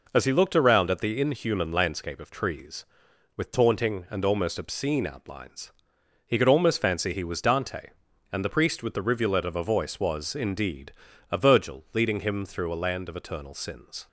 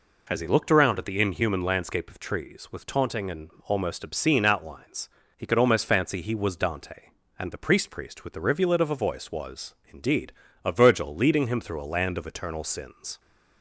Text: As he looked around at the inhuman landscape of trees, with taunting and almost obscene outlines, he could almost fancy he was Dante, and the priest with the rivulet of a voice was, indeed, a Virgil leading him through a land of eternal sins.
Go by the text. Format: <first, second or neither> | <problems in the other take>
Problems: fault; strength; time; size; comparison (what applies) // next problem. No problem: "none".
first | pauses between "and" and "almost"; slight; at 3.4 s; 0.16 s long // says "priest" twice; at 7.8 s